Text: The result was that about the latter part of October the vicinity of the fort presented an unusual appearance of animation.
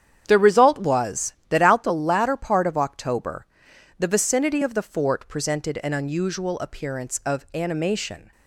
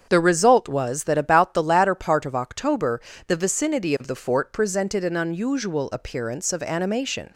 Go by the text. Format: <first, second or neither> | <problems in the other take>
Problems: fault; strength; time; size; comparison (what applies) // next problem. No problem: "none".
second | starts louder than the rest; strong; until 1.2 s; 9 dB; strong in the second // says "out" for "about"; at 1.6 s // pauses between "October" and "the"; noticeable; at 3.4 s; 0.52 s long; slight in the second